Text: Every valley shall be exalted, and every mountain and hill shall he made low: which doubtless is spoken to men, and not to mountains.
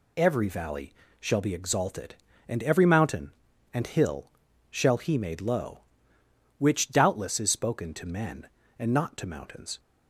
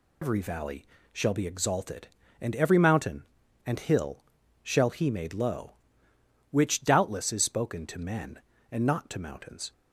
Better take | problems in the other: first | loses the start of "Every"; at 0.2 s; 120 ms // pauses between "valley" and "shall"; slight; at 0.8 s; 0.28 s long; slight in the first // pauses between "hill" and "shall"; at 4.2 s; 0.38 s long; also in the first

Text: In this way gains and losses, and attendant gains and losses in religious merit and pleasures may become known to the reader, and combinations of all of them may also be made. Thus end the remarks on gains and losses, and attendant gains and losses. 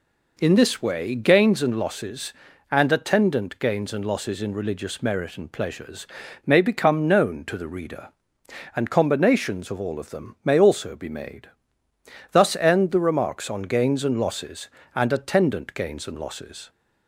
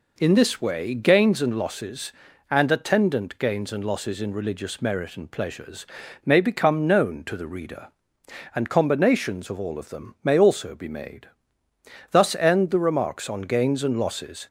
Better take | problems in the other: first | pauses between "pleasures" and "may"; at 5.8 s; 0.40 s long; also in the first // stops before "and attendant gains and losses"; at 14.4 s

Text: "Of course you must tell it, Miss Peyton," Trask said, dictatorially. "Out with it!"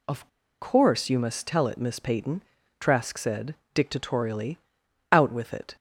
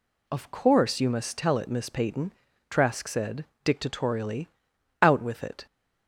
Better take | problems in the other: second | pauses between "Of" and "course"; slight; at 0.2 s; 0.33 s long

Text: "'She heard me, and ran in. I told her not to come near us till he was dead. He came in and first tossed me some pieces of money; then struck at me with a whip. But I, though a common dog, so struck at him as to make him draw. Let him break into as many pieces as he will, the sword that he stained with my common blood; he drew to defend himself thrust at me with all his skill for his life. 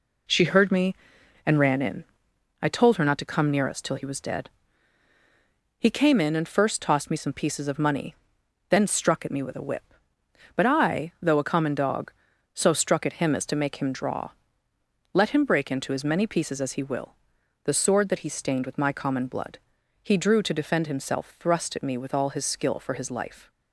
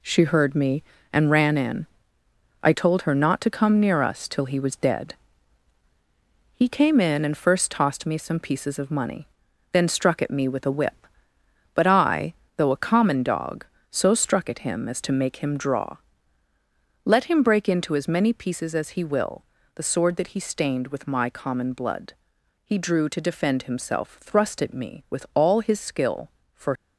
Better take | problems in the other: first | stops before "his life"; at 26.7 s

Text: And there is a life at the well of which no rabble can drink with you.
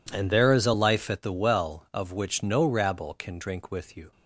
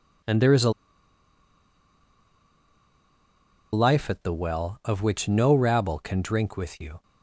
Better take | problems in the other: first | pauses between "a" and "life"; strong; at 0.7 s; 3.0 s long

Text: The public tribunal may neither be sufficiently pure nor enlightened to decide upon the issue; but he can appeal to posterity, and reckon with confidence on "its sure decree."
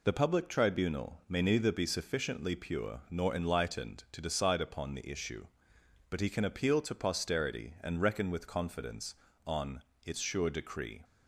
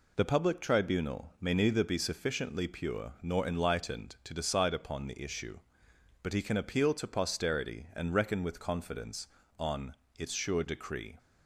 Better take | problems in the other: neither | pauses between "on" and "its"; slight; the same in both

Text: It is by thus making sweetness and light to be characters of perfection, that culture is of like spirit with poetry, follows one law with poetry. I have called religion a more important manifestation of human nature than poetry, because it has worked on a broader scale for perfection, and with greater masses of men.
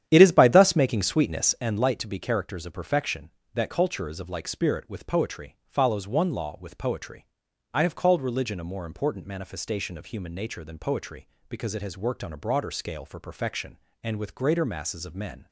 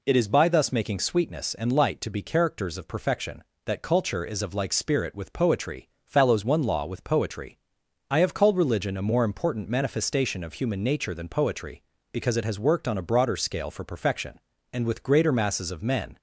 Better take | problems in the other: second | starts louder than the rest; strong; until 1.7 s; 10 dB

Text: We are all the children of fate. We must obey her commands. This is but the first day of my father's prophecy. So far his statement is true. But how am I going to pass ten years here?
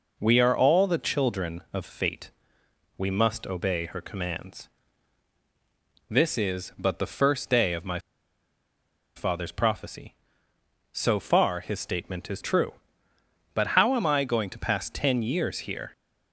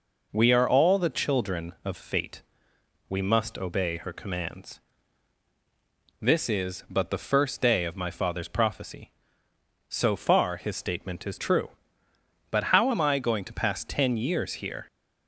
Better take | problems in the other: second | pauses between "my" and "father's"; at 7.9 s; 1.1 s long

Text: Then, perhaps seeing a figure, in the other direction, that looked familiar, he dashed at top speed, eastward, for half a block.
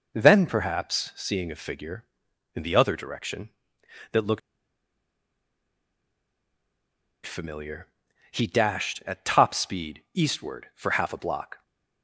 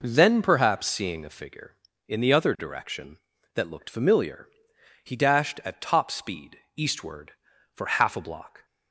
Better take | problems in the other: second | pauses between "looked" and "familiar"; strong; at 4.3 s; 2.8 s long

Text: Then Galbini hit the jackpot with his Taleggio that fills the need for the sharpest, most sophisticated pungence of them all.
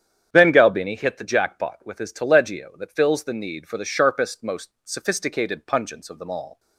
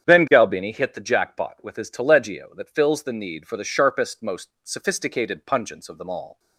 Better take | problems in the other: neither | starts louder than the rest; strong; the same in both // pauses between "most" and "sophisticated"; slight; the same in both

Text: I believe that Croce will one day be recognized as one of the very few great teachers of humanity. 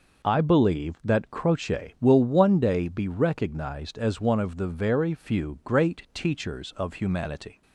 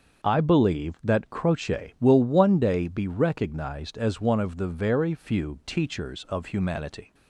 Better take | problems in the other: first | starts louder than the rest; until 1.3 s; 6.5 dB // skips "great"; at 5.6 s

